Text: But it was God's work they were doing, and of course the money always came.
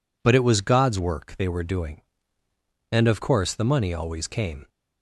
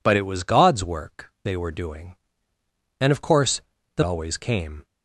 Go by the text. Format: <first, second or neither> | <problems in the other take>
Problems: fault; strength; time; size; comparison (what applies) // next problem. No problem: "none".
first | pauses between "course" and "the"; slight; at 3.6 s; 0.36 s long // skips "money"; at 4.0 s